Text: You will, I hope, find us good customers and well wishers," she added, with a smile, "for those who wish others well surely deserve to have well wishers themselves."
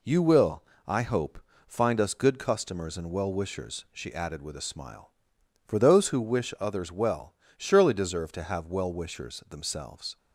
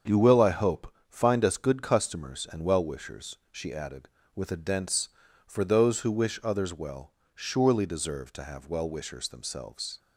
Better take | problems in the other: first | starts louder than the rest; until 1.2 s; 7 dB // says "dense" for "smile"; at 4.5 s // pauses between "well" and "surely"; slight; at 7.1 s; 0.24 s long; slight in the first

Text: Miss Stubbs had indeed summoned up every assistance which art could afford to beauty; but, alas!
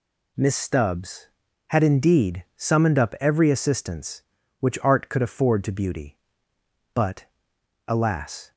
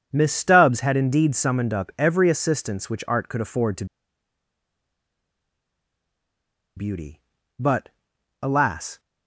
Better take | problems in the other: first | pauses between "to" and "beauty"; strong; at 3.8 s; 2.9 s long

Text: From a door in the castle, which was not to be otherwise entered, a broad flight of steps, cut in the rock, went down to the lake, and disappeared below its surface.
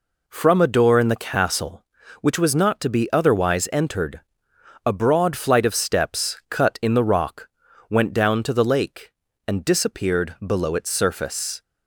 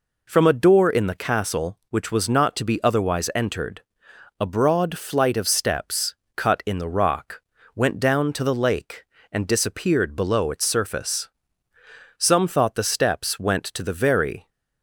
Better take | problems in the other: first | goes on to say "Some thought the steps went to the very"; strong; from 12.1 s on; 2.3 s long

